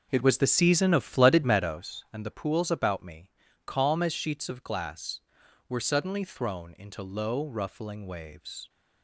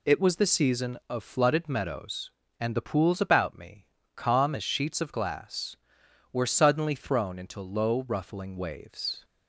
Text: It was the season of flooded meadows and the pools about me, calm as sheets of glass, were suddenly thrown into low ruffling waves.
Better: second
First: starts louder than the rest; noticeable; until 1.9 s; 5.5 dB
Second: none

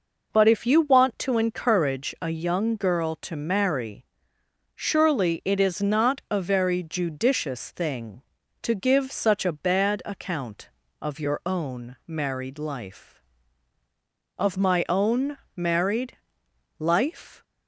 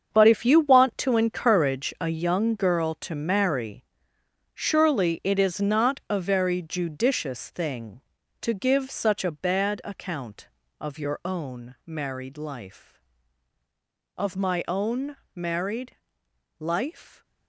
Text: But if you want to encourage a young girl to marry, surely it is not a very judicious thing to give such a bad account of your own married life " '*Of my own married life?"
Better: first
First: pauses between "own" and "married"; slight; at 15.3 s; 0.20 s long // pauses between "married" and "life"; noticeable; at 16.1 s; 0.60 s long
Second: gets quieter; strong; throughout; 17.5 dB // pauses between "own" and "married"; slight; at 15.1 s; 0.20 s long // pauses between "married" and "life"; noticeable; at 15.9 s; 0.62 s long

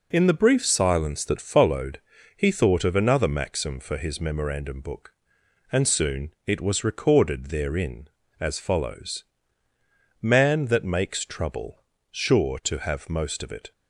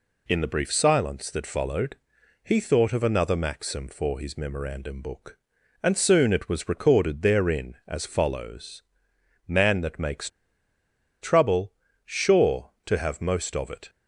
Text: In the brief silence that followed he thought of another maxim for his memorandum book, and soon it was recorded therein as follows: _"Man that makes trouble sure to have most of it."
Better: first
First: pauses between "followed" and "he"; slight; at 2.0 s; 0.34 s long // pauses between "trouble" and "sure"; slight; at 11.8 s; 0.26 s long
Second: pauses between "followed" and "he"; noticeable; at 1.9 s; 0.46 s long // pauses between "makes" and "trouble"; noticeable; at 10.2 s; 0.93 s long // pauses between "trouble" and "sure"; slight; at 11.7 s; 0.32 s long

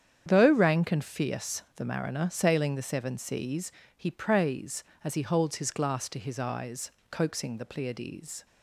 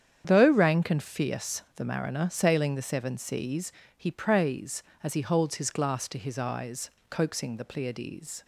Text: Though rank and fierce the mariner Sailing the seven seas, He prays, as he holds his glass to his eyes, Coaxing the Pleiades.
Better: neither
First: starts louder than the rest; strong; until 1.2 s; 8.5 dB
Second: starts louder than the rest; strong; until 1.2 s; 8.5 dB

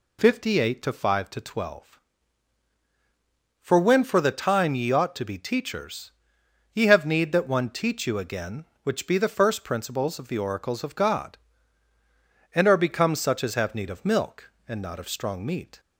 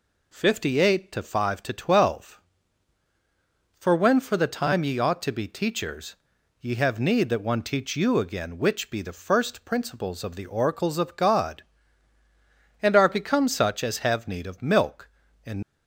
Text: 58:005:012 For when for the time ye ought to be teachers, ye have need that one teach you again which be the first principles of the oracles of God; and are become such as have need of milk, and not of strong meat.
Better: first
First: none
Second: stops before "not of strong meat"; at 15.6 s

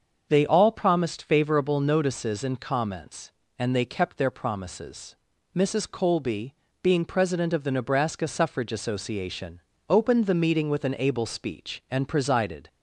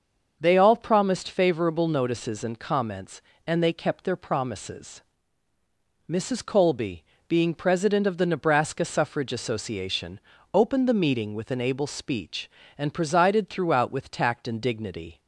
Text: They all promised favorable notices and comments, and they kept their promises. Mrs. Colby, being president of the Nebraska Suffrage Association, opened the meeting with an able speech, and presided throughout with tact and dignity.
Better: second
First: starts louder than the rest; until 1.3 s; 6.5 dB // stops before "throughout with tact and dignity"; at 12.6 s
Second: starts louder than the rest; until 1.4 s; 6 dB

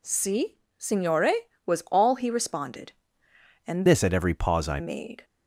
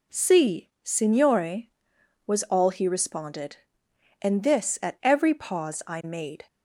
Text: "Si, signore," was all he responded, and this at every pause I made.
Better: second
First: changes voice from "this" to "I"; from 3.8 to 4.7 s; 0.9 s long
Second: none

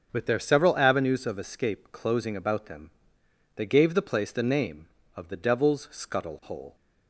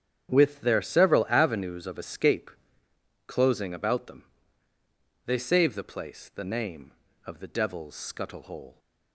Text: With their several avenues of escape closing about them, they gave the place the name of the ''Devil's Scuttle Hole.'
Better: first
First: starts louder than the rest; until 1.1 s; 6.5 dB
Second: starts louder than the rest; strong; until 1.3 s; 8.5 dB // pauses between "escape" and "closing"; noticeable; at 2.5 s; 0.74 s long // says "save" for "gave"; at 5.3 s

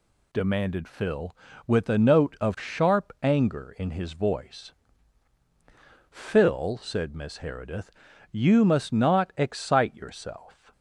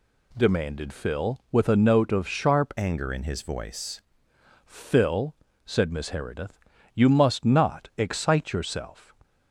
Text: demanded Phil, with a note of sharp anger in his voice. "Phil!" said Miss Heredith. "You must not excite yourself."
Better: first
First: none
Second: changes voice from "anger" to "voice"; from 2.7 to 4.0 s; 1.3 s long

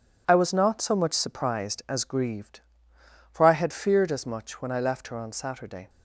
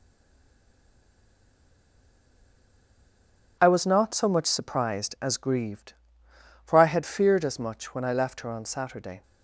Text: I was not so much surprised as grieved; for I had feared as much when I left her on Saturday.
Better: first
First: none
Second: stays silent before the first word; strong; until 3.5 s; 3.5 s long

